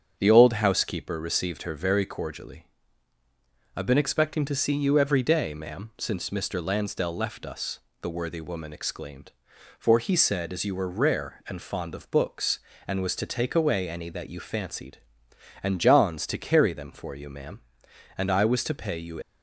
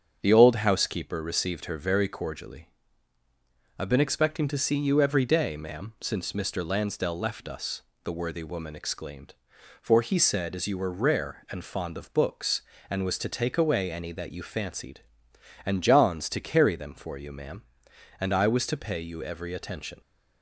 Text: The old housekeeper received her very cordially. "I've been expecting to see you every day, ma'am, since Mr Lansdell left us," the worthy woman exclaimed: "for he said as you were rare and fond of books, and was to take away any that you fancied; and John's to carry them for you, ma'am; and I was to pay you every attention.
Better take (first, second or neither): second